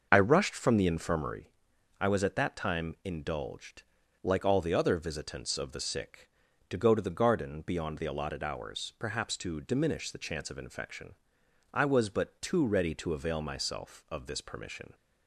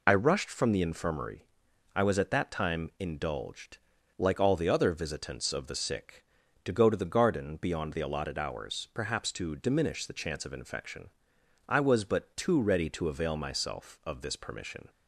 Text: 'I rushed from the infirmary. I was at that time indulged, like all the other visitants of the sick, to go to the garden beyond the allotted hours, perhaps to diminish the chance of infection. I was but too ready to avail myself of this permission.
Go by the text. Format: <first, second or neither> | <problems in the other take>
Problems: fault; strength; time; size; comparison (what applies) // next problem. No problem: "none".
second | starts louder than the rest; noticeable; until 1.5 s; 5.5 dB